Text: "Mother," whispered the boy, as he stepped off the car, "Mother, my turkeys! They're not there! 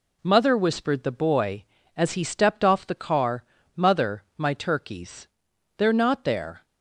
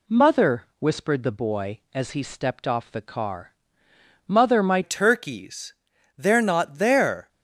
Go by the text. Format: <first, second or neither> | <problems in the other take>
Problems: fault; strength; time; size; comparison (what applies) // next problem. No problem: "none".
first | changes voice at "turkeys"; from 4.8 s on; 2.4 s long